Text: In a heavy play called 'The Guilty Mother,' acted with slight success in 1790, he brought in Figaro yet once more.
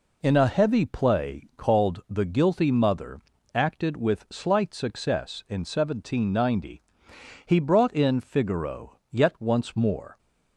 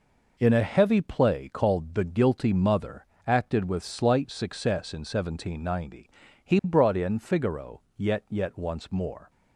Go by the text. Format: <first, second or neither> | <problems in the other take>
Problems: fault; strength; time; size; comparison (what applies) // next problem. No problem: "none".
first | pauses between "Figaro" and "yet"; slight; at 7.7 s; 0.16 s long // says "yet" twice; at 8.2 s